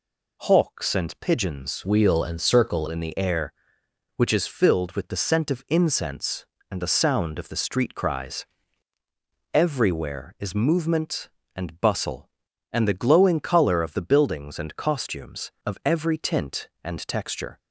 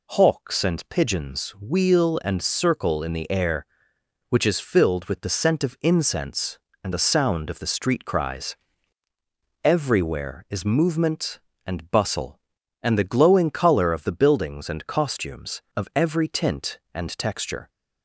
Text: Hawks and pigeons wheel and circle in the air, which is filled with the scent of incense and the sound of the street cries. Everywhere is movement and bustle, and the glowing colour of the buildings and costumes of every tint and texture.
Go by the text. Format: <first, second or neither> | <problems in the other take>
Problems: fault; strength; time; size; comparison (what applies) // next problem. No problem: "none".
second | changes voice from "wheel" to "circle"; from 1.8 to 2.8 s; 1.0 s long